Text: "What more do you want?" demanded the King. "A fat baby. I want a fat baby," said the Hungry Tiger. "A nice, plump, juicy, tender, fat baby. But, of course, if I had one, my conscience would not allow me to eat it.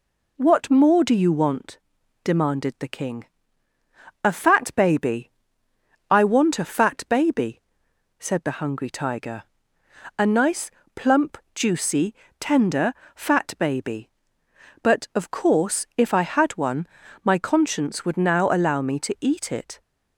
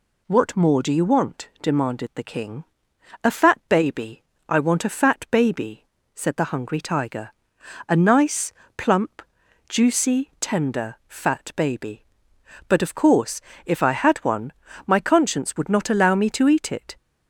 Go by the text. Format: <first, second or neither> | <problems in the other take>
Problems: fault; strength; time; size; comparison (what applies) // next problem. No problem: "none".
second | says "now" for "not"; at 18.1 s